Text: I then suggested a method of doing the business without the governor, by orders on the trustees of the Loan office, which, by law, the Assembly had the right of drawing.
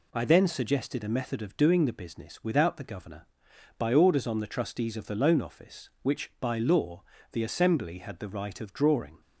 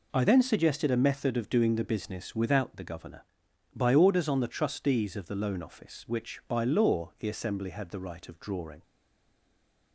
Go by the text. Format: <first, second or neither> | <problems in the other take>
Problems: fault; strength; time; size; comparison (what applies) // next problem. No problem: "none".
first | stays silent after the last word; from 8.8 s on; 1.1 s long